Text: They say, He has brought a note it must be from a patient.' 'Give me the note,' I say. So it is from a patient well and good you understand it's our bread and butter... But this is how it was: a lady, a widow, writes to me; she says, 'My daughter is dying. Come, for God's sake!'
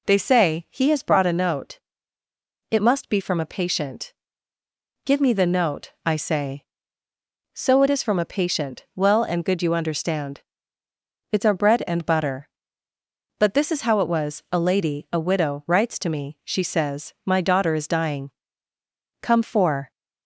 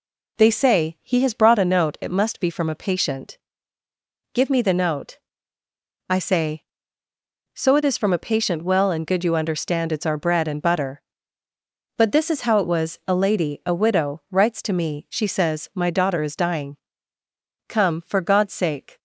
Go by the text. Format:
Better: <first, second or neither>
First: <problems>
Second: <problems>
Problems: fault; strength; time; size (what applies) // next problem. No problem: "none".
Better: second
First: pauses between "note" and "it"; noticeable; at 1.7 s; 0.92 s long // pauses between "understand" and "it's"; noticeable; at 10.4 s; 0.92 s long // stops before "God's sake"; at 19.9 s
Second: none